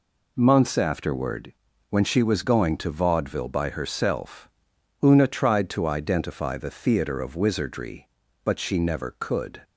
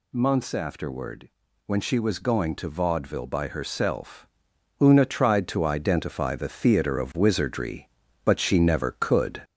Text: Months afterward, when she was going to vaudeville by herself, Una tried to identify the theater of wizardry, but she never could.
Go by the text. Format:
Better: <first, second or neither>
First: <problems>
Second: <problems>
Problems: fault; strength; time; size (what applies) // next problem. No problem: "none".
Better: first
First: none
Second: gets louder; slight; throughout; 3 dB